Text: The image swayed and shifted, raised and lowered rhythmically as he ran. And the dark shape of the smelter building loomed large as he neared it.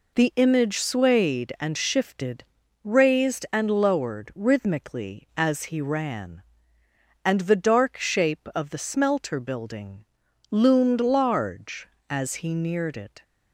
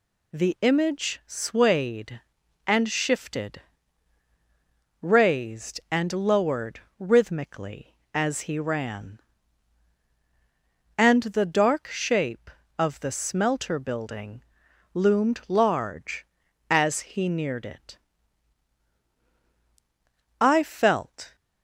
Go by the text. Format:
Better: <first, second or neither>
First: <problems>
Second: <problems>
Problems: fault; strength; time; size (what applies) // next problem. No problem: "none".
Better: first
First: pauses between "building" and "loomed"; noticeable; at 10.0 s; 0.46 s long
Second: pauses between "lowered" and "rhythmically"; slight; at 6.8 s; 0.18 s long // pauses between "building" and "loomed"; noticeable; at 14.4 s; 0.50 s long // goes on to say "I felt"; noticeable; from 20.4 s on; 0.94 s long